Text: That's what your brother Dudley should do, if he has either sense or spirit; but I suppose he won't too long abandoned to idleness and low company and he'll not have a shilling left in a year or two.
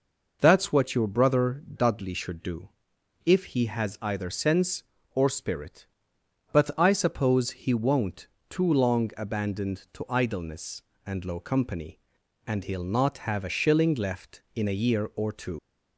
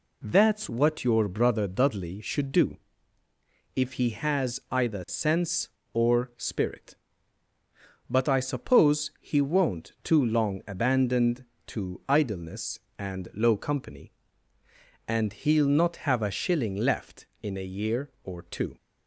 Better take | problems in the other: second | pauses between "won't" and "too"; slight; at 8.2 s; 0.24 s long // leaves "two" unfinished; at 15.5 s; 75 ms

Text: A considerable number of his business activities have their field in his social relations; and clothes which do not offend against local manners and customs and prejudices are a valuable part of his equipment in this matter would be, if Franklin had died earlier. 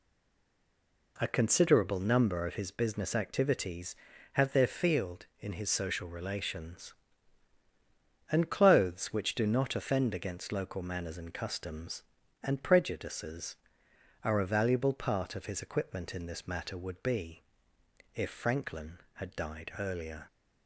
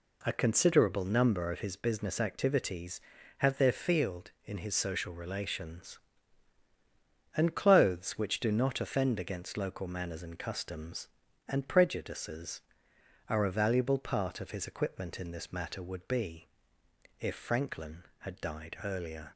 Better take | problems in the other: second | stays silent before the first word; until 1.1 s; 1.1 s long

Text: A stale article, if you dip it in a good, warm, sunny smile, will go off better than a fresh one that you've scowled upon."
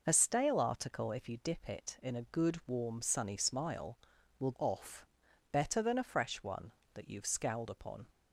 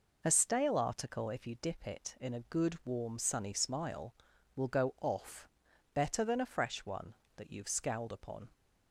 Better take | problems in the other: second | skips "go"; at 4.5 s // pauses between "off" and "better"; noticeable; at 5.0 s; 0.46 s long; noticeable in the second

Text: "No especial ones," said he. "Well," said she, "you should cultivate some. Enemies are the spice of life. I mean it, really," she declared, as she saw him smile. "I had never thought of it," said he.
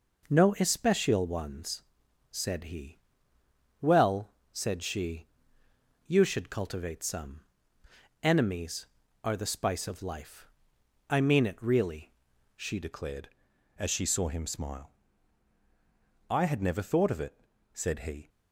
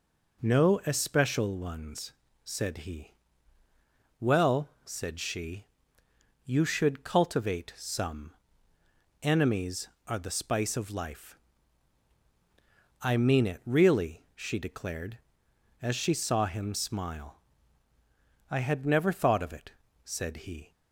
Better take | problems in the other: second | changes voice at "declared"; from 12.8 s on; 5.4 s long

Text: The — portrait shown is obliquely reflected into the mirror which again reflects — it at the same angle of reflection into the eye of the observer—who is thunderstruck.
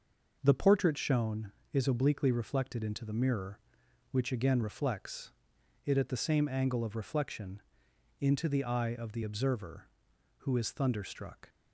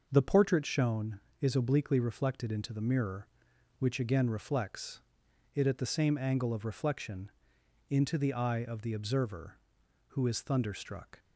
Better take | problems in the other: neither | pauses between "reflection" and "into"; noticeable; the same in both

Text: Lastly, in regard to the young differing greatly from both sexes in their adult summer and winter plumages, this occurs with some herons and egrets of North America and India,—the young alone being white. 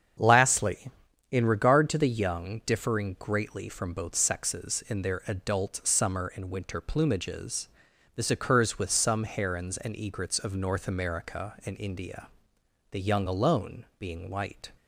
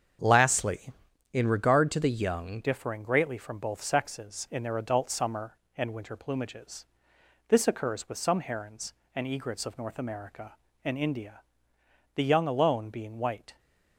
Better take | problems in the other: first | starts louder than the rest; strong; until 1.6 s; 7.5 dB; strong in the first // changes voice at "differing"; from 2.6 s on; 10.9 s long

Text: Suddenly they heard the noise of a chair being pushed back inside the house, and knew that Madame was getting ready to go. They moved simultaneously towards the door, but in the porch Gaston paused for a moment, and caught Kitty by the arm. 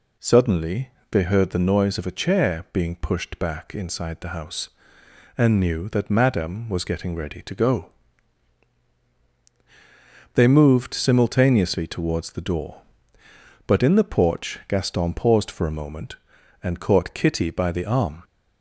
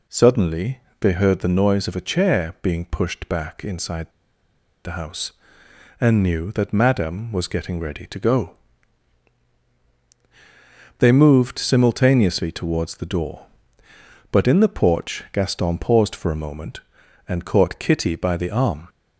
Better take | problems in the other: first | pauses between "Suddenly" and "they"; slight; at 0.7 s; 0.20 s long; slight in the first // pauses between "inside" and "the"; noticeable; at 4.0 s; 0.75 s long

